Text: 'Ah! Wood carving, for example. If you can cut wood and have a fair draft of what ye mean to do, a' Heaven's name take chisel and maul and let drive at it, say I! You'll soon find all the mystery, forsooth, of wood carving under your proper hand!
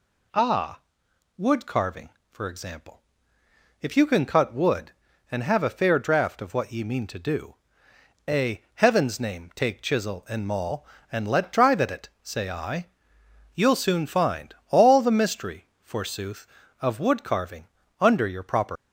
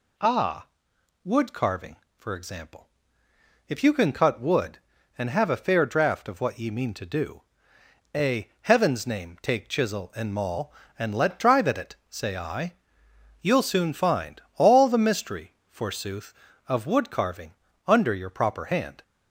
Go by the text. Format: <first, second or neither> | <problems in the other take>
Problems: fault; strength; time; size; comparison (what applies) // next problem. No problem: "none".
second | pauses between "carving" and "under"; slight; at 17.6 s; 0.34 s long; slight in the second // stops before "hand"; at 18.7 s